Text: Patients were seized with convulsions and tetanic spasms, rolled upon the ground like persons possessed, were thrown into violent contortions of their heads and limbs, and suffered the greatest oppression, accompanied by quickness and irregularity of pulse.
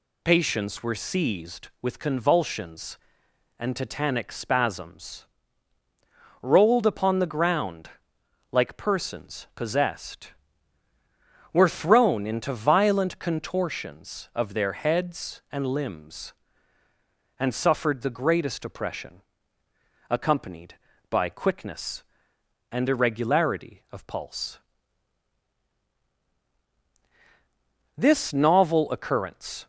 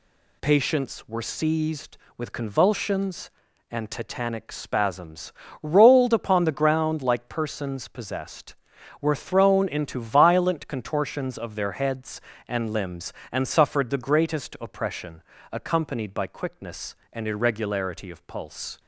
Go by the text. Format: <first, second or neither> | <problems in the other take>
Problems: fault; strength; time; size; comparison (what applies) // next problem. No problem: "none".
second | pauses between "ground" and "like"; noticeable; at 7.8 s; 0.64 s long // goes on to say "This novel occurrence"; strong; from 27.9 s on; 1.7 s long